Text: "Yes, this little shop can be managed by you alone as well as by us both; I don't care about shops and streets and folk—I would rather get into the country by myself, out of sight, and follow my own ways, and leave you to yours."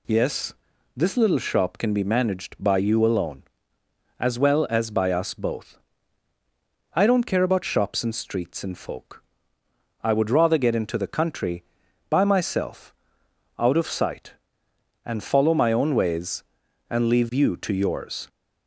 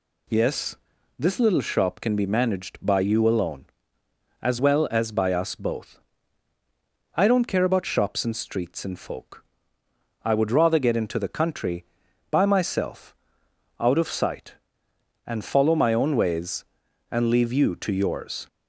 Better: neither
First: none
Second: none

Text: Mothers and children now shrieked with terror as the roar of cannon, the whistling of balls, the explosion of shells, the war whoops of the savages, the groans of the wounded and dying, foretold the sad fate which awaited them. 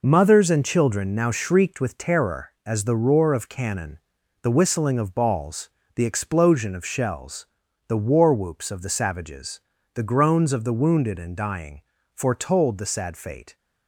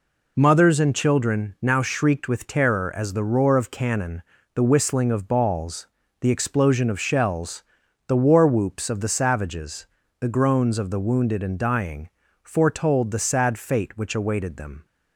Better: second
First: stops before "which awaited them"; at 13.5 s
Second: none

